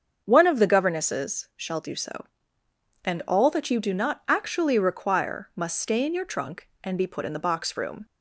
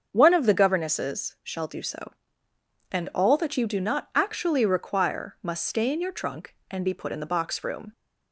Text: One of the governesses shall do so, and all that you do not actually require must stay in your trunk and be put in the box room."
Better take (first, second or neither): neither